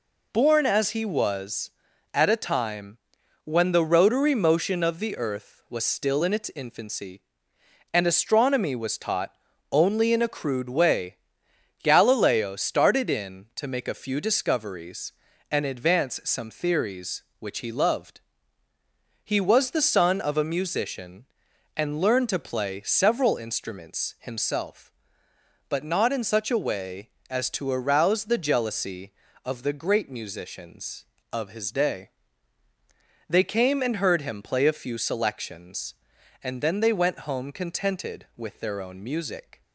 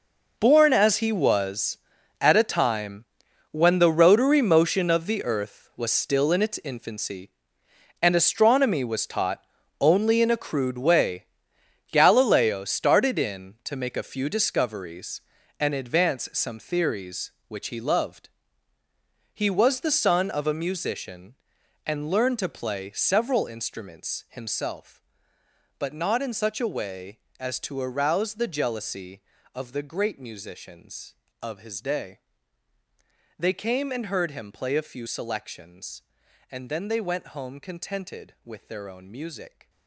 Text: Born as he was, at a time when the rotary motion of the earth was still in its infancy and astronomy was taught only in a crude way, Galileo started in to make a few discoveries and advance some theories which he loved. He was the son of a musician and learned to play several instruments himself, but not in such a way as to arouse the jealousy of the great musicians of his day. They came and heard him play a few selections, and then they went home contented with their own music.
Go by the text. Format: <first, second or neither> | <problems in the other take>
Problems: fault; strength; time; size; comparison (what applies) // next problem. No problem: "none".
first | gets quieter; strong; throughout; 14 dB // pauses between "time" and "when"; at 3.0 s; 0.44 s long; also in the first // pauses between "taught" and "only"; at 9.4 s; 0.38 s long; also in the first